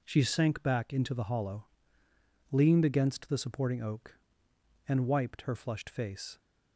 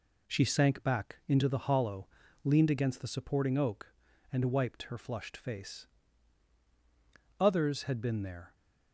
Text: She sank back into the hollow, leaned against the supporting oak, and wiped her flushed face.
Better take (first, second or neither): first